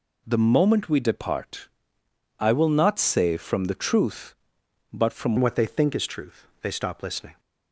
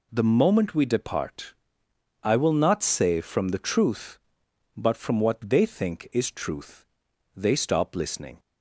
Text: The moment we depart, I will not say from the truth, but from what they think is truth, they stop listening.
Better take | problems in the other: second | changes voice at "what"; from 5.3 s on; 2.0 s long

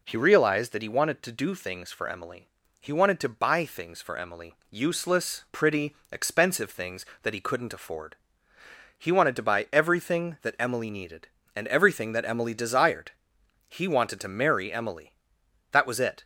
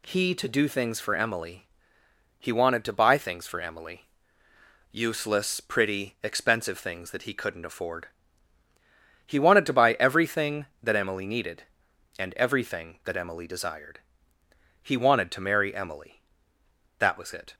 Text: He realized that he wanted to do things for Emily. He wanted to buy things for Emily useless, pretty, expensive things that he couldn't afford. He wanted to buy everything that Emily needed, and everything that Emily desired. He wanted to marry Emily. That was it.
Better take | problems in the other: first | skips "realized that he wanted"; at 0.3 s // pauses between "Emily" and "useless"; noticeable; at 4.0 s; 0.88 s long; slight in the first

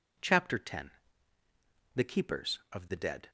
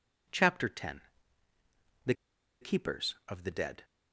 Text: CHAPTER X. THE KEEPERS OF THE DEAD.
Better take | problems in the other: first | pauses between "THE" and "KEEPERS"; noticeable; at 2.1 s; 0.47 s long

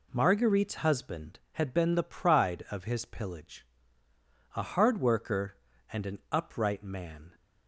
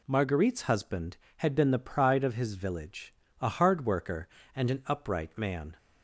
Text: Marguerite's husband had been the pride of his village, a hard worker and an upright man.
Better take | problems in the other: second | says "pillage" for "village"; at 3.0 s

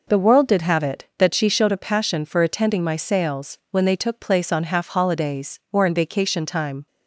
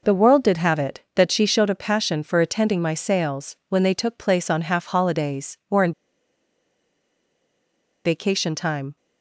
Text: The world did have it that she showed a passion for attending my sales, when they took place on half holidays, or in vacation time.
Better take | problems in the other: first | pauses between "in" and "vacation"; strong; at 5.9 s; 2.1 s long

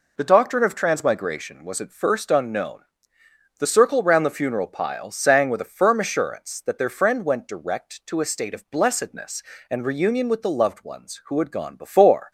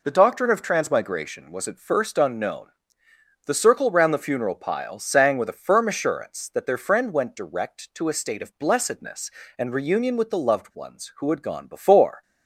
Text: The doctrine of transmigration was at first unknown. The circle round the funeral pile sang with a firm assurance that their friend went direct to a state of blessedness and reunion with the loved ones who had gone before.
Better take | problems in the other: neither | none

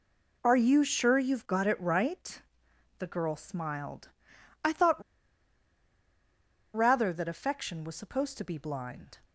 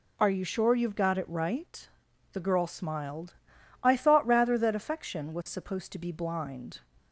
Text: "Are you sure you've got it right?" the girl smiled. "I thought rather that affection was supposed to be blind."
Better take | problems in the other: second | pauses between "thought" and "rather"; strong; at 5.0 s; 1.7 s long

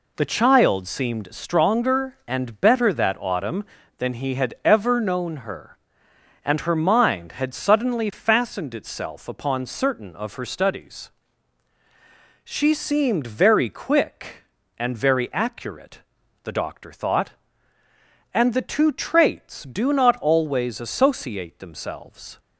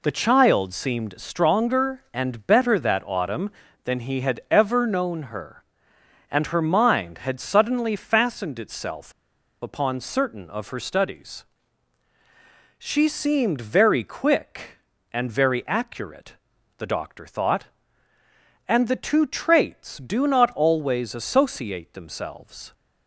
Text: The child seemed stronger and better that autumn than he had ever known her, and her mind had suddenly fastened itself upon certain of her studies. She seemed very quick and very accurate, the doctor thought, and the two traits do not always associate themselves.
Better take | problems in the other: first | pauses between "itself" and "upon"; noticeable; at 9.1 s; 0.50 s long

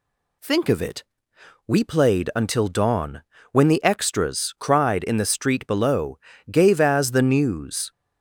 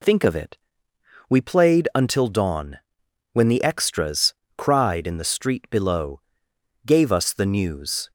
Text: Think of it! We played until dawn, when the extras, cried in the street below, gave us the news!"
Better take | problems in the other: second | says "as" for "us"; at 6.8 s

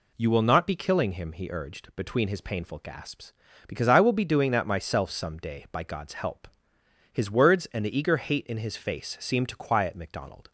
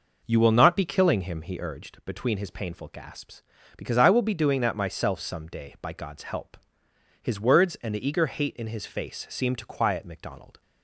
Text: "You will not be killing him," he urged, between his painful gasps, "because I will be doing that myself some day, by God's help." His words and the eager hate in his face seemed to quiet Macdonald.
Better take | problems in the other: first | starts louder than the rest; noticeable; until 1.8 s; 5.5 dB

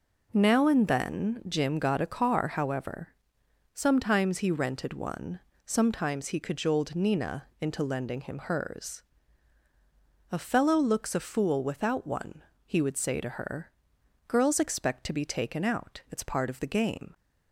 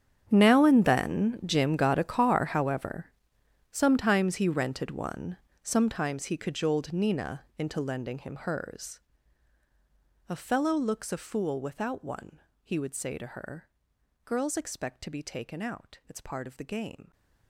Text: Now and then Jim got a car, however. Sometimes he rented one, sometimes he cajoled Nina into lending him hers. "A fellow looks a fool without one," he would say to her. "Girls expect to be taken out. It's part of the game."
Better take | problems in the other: first | gets quieter; strong; throughout; 19 dB

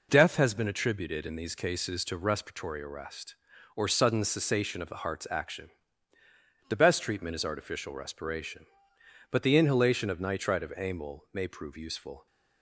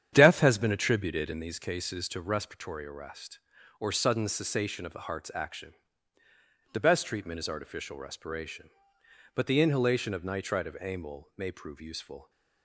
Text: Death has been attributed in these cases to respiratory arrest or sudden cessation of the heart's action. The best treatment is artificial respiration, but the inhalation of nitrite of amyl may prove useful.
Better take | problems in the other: first | starts louder than the rest; strong; until 1.6 s; 9 dB

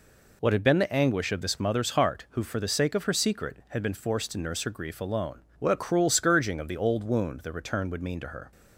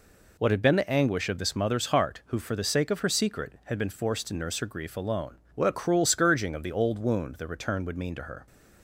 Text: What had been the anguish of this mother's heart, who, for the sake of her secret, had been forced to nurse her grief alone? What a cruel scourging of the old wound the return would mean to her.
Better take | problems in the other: neither | none

